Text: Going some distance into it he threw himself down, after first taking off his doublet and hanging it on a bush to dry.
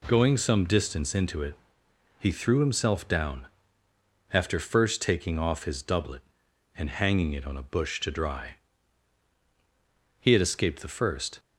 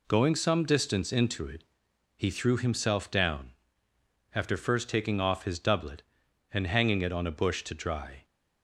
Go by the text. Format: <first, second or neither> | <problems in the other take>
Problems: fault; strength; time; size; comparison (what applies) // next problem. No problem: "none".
second | pauses between "it" and "he"; noticeable; at 1.5 s; 0.64 s long; noticeable in the second // goes on to say "He had escaped the first"; noticeable; from 10.1 s on; 1.2 s long